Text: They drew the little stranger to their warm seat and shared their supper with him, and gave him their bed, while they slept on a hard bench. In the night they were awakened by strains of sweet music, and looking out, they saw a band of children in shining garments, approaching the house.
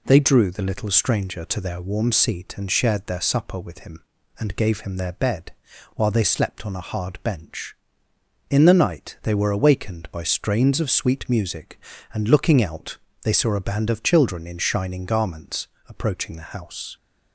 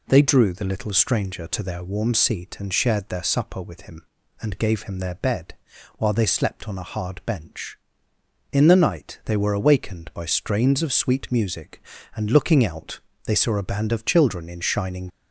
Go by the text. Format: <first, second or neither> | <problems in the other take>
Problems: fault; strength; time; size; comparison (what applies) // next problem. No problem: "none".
first | stops before "garments approaching the house"; at 15.0 s